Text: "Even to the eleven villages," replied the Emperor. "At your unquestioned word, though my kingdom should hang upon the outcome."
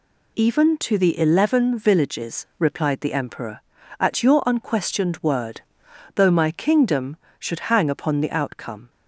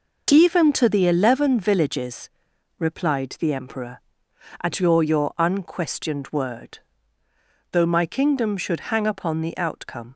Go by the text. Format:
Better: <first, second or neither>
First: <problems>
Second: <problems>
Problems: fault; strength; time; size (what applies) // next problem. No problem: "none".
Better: first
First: none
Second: says "your" twice; at 5.0 s